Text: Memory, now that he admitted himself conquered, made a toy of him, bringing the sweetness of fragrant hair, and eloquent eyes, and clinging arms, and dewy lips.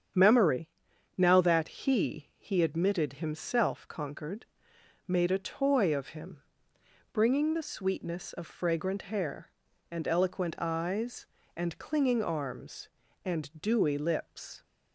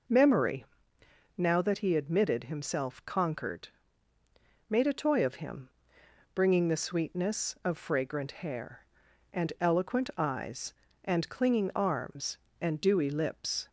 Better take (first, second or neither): second